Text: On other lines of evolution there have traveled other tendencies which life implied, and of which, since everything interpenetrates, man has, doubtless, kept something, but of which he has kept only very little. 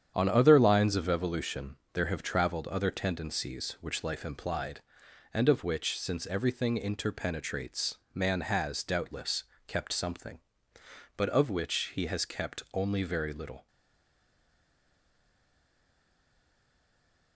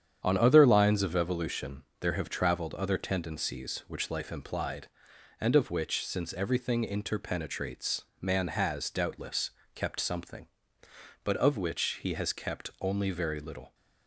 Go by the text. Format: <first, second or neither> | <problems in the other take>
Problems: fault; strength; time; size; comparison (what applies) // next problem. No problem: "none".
second | starts louder than the rest; strong; until 1.1 s; 8.5 dB; strong in the second // pauses between "evolution" and "there"; slight; at 1.7 s; 0.18 s long; slight in the second // stays silent after the last word; strong; from 13.6 s on; 3.7 s long